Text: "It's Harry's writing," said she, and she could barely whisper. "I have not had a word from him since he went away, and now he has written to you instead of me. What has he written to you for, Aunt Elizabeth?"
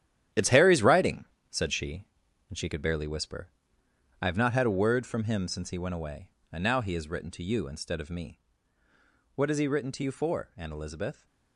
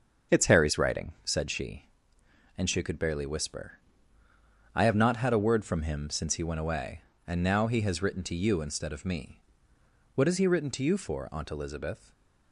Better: second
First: gets quieter; strong; throughout; 10.5 dB // starts louder than the rest; strong; until 1.5 s; 11 dB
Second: starts louder than the rest; until 1.4 s; 6.5 dB

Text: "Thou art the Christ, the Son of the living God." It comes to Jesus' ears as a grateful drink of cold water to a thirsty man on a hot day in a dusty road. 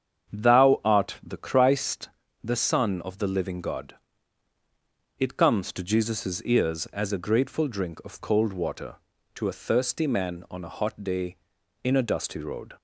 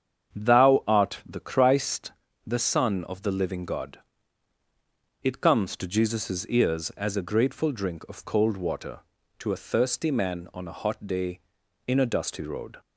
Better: neither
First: starts louder than the rest; strong; until 1.4 s; 8 dB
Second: starts louder than the rest; strong; until 1.4 s; 8 dB

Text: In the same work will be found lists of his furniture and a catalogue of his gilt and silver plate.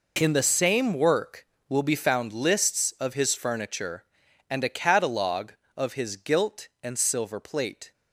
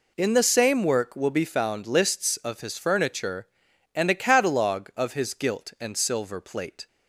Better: neither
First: none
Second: none

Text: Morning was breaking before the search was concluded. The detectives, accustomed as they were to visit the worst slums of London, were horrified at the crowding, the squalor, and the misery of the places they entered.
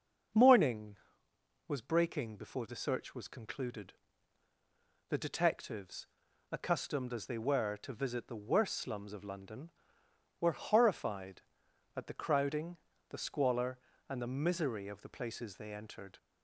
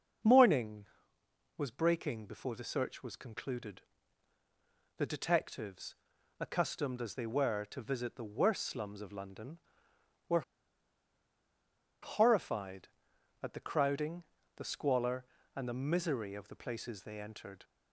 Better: first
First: starts louder than the rest; until 2.0 s; 6.5 dB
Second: starts louder than the rest; until 1.9 s; 6.5 dB // pauses between "were" and "horrified"; strong; at 10.4 s; 1.6 s long

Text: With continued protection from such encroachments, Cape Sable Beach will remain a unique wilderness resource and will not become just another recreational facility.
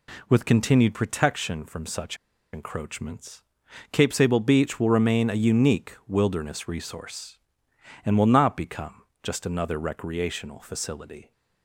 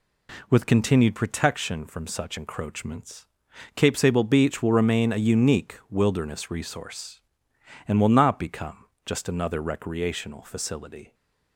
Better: second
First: pauses between "such" and "encroachments"; at 2.1 s; 0.36 s long // pauses between "become" and "just"; slight; at 9.0 s; 0.22 s long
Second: pauses between "become" and "just"; slight; at 8.8 s; 0.22 s long

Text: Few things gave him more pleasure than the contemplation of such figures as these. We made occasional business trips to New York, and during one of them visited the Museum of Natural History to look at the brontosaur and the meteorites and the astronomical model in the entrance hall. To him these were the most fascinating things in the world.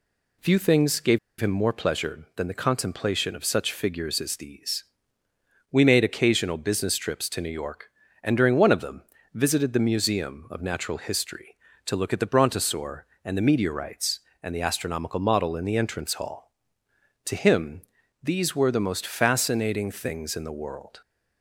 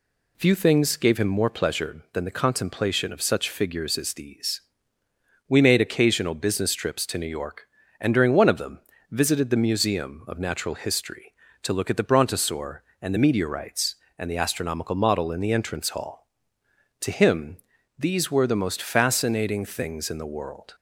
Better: second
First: pauses between "gave" and "him"; slight; at 1.1 s; 0.20 s long // pauses between "them" and "visited"; slight; at 9.0 s; 0.30 s long // pauses between "him" and "these"; at 17.8 s; 0.40 s long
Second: pauses between "them" and "visited"; slight; at 8.7 s; 0.30 s long // pauses between "him" and "these"; at 17.5 s; 0.40 s long

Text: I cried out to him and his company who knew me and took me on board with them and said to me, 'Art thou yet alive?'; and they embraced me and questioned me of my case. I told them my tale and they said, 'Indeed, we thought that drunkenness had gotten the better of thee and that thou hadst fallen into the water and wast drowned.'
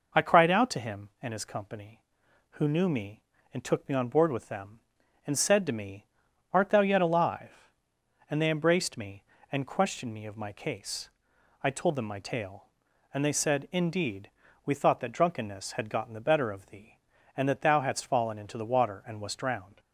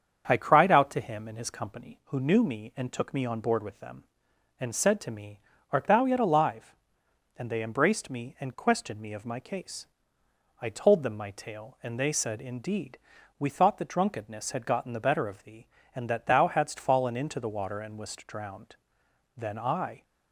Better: first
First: none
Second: starts louder than the rest; strong; until 1.2 s; 7.5 dB // goes on to say "Then I"; noticeable; from 19.3 s on; 0.68 s long

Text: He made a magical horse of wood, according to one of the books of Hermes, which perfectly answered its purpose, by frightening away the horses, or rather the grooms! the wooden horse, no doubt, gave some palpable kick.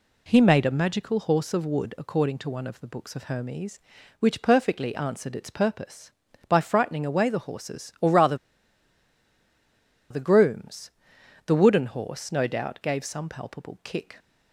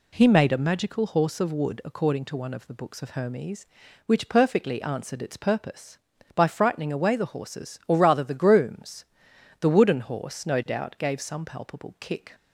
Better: second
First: pauses between "rather" and "the"; strong; at 8.3 s; 1.7 s long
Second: none

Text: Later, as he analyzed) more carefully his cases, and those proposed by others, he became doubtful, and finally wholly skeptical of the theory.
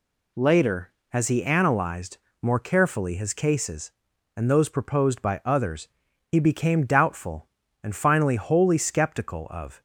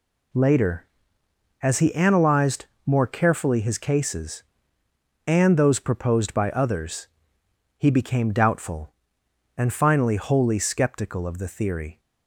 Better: second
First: stops before "the theory"; at 9.7 s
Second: none

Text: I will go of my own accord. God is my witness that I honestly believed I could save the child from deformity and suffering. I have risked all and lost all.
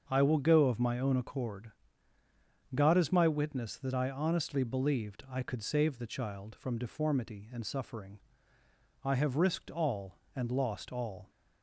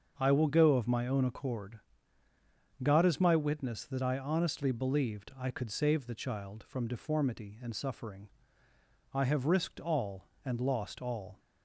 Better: neither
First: starts louder than the rest; until 1.0 s; 6.5 dB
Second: starts louder than the rest; until 1.1 s; 6.5 dB

